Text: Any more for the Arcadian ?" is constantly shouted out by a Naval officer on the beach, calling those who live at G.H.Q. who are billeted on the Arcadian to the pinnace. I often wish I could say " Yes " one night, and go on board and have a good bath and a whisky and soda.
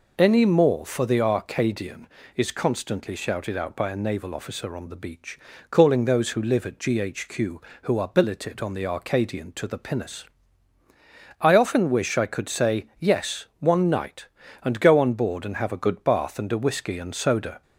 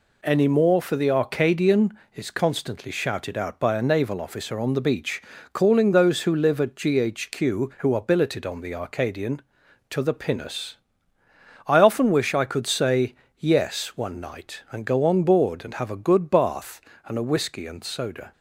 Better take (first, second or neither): neither